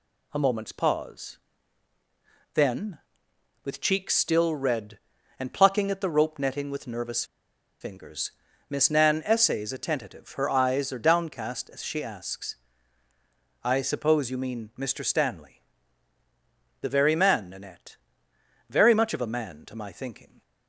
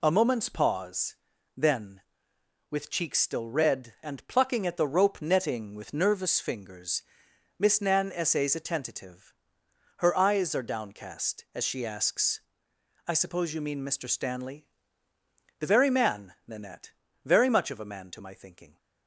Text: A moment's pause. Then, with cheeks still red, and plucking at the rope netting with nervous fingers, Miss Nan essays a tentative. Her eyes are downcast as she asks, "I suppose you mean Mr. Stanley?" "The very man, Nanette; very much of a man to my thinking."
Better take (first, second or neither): second